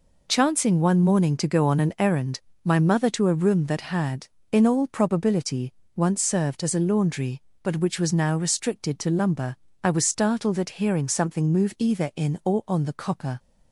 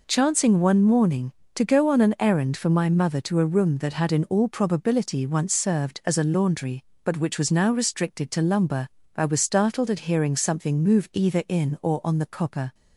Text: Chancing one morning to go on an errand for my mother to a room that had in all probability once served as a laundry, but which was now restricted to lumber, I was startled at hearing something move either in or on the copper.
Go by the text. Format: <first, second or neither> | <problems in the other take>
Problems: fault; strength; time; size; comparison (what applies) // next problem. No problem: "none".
second | skips "for"; at 2.5 s // pauses between "probability" and "once"; slight; at 5.7 s; 0.22 s long